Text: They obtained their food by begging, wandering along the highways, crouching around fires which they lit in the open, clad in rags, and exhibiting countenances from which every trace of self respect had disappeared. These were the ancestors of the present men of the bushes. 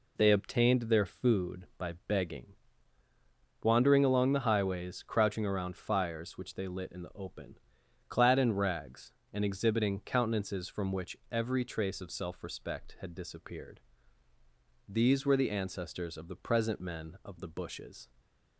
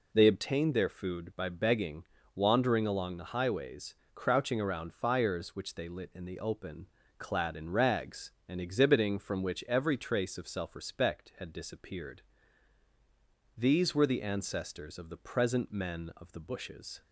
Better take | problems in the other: first | skips "countenances"; at 9.1 s

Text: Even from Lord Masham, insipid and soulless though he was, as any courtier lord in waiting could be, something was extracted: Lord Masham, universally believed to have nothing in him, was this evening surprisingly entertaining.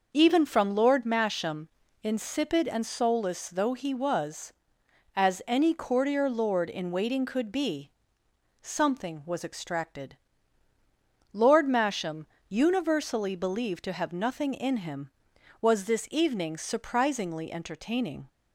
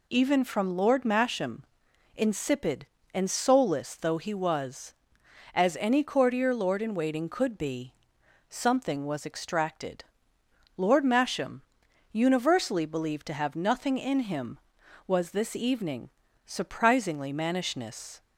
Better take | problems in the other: first | pauses between "evening" and "surprisingly"; slight; at 16.0 s; 0.36 s long // says "mannishness" for "entertaining"; at 17.3 s

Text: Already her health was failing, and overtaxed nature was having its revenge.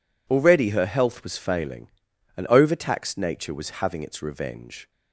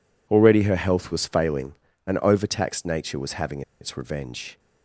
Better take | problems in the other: first | pauses between "having" and "its"; slight; at 3.6 s; 0.19 s long

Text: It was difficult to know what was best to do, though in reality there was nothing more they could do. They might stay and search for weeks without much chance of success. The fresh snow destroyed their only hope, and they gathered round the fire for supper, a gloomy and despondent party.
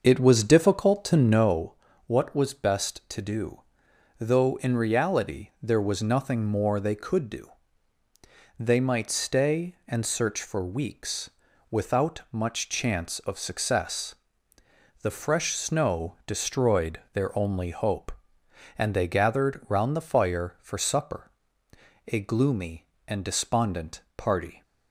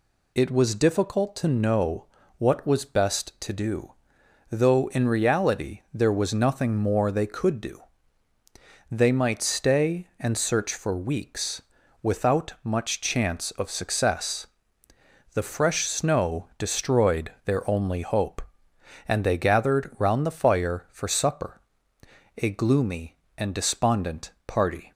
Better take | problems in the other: second | starts louder than the rest; until 1.6 s; 6 dB // pauses between "know" and "what"; slight; at 1.7 s; 0.32 s long; slight in the second // pauses between "weeks" and "without"; at 11.2 s; 0.40 s long; also in the second

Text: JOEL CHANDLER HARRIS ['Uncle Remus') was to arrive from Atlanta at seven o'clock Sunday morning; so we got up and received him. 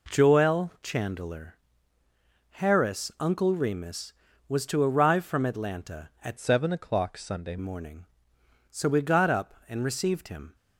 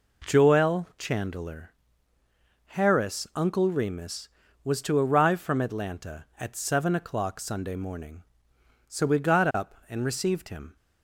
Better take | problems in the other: second | pauses between "CHANDLER" and "HARRIS"; noticeable; at 1.5 s; 0.94 s long; noticeable in the second // changes voice from "seven" to "Sunday"; from 6.3 to 7.5 s; 1.2 s long

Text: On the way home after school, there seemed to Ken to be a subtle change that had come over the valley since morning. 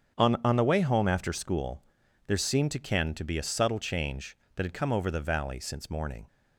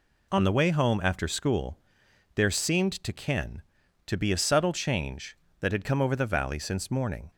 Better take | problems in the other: second | starts louder than the rest; strong; until 1.2 s; 8 dB // says "On" twice; at 0.4 s

